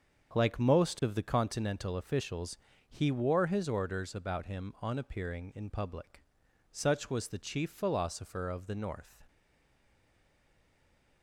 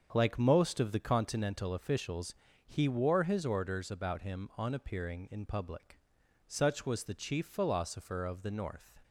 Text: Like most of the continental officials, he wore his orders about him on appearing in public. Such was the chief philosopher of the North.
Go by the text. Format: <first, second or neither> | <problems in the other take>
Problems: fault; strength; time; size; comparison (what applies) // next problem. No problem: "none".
second | starts louder than the rest; strong; until 1.3 s; 7 dB; also in the second // stays silent after the last word; noticeable; from 9.2 s on; 2.0 s long